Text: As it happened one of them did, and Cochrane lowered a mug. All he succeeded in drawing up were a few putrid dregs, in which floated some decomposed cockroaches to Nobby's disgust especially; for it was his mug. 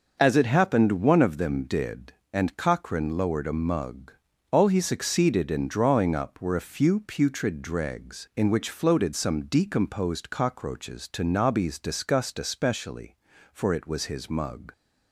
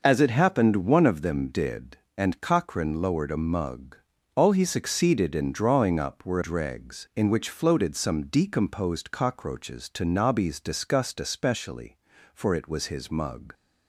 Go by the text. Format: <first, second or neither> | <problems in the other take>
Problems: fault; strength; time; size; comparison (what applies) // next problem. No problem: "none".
first | skips "a few putrid"; at 6.4 s